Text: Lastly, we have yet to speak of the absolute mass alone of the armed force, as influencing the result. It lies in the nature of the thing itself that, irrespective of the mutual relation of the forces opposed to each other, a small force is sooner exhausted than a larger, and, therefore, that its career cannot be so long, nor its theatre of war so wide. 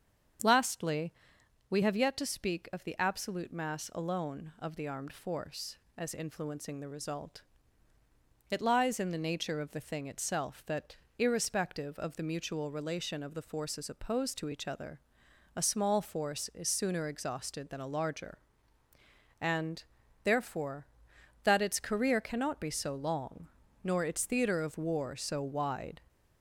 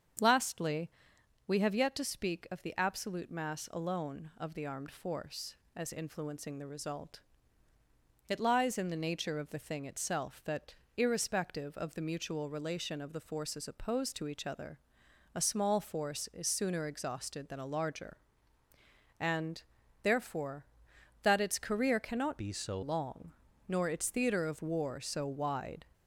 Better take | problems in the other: first | starts louder than the rest; strong; until 1.7 s; 7 dB; strong in the first // changes voice from "be" to "so"; from 22.3 to 22.8 s; 0.5 s long

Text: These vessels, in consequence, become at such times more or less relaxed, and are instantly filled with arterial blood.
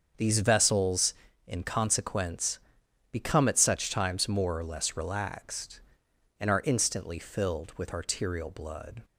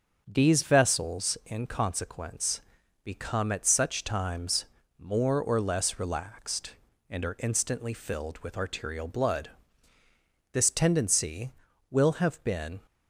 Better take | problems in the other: first | starts louder than the rest; until 1.2 s; 6.5 dB; also in the first // pauses between "times" and "more"; slight; at 4.6 s; 0.34 s long // goes on to say "This tendency will have been"; strong; from 10.5 s on; 2.2 s long

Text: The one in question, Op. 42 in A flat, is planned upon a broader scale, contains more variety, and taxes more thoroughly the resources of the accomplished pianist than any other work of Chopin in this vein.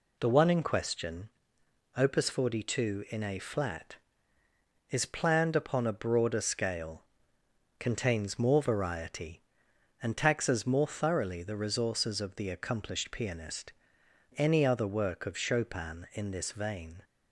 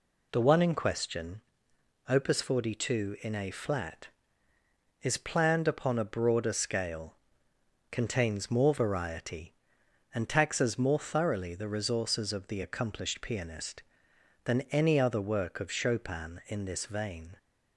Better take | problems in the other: second | skips "than"; at 14.0 s

